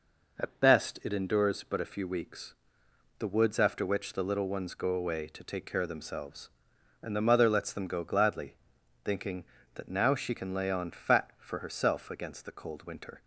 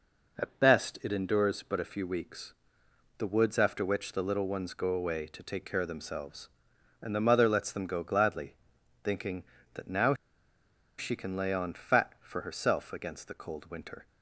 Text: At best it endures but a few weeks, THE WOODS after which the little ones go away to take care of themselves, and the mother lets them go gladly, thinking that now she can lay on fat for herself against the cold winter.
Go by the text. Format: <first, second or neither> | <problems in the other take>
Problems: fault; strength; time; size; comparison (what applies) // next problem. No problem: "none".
first | pauses between "now" and "she"; noticeable; at 10.1 s; 0.84 s long